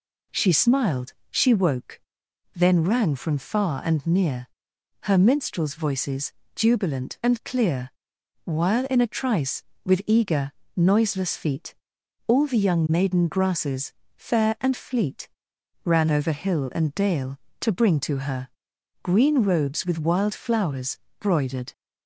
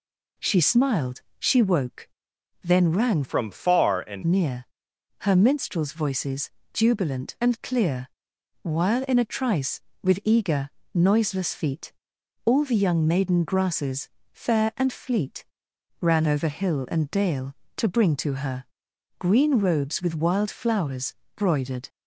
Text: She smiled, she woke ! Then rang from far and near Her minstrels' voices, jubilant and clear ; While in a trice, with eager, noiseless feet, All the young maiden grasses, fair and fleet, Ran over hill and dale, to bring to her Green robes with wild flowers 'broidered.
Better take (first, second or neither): first